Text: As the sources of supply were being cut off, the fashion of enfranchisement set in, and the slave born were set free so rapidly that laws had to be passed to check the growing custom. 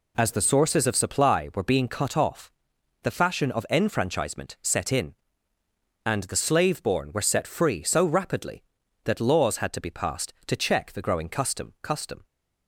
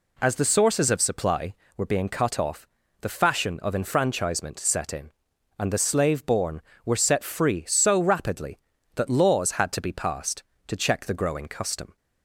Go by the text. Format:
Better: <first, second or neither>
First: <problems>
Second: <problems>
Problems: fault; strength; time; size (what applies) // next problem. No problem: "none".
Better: second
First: says "custom" twice; at 11.8 s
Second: none